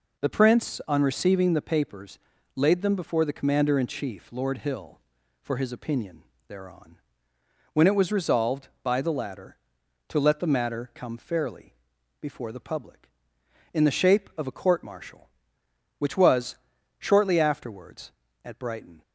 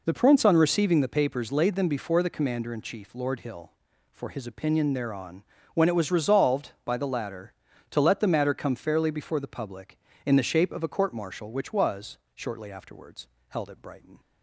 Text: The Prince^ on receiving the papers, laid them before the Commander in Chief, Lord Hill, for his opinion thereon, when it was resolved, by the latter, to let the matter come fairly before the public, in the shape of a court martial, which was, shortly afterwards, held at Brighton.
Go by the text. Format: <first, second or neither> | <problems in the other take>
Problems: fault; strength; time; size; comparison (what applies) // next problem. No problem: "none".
second | pauses between "opinion" and "thereon"; slight; at 6.2 s; 0.24 s long // pauses between "fairly" and "before"; at 11.7 s; 0.44 s long // skips "held"; at 18.2 s